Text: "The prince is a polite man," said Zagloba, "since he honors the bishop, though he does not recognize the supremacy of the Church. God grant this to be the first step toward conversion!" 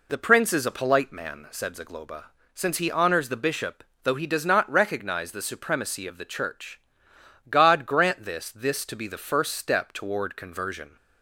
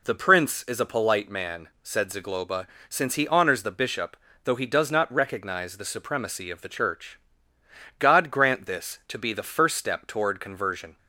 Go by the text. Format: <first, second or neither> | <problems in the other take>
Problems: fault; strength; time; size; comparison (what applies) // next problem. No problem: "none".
second | says "this" twice; at 8.4 s